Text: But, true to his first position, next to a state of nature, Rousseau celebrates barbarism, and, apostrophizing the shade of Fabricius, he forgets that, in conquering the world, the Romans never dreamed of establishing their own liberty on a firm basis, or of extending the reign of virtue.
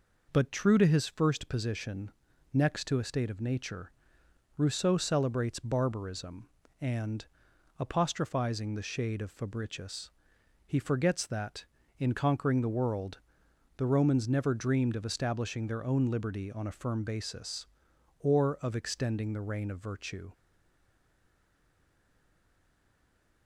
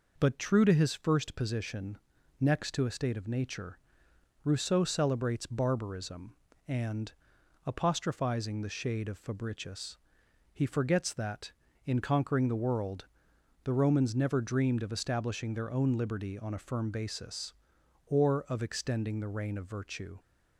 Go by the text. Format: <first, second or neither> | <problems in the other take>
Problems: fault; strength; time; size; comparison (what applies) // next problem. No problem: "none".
second | stays silent after the last word; strong; from 20.3 s on; 3.1 s long